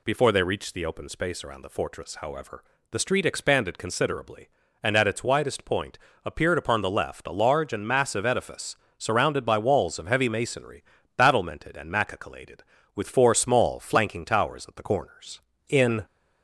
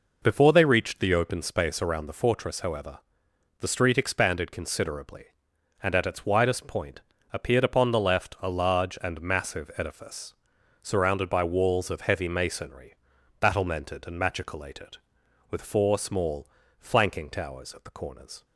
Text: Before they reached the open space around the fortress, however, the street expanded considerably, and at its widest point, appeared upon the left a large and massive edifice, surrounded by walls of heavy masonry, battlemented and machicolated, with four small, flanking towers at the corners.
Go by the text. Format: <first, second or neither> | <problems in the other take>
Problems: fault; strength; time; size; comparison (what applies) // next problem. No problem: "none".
second | goes on to say "In"; slight; from 15.6 s on; 0.36 s long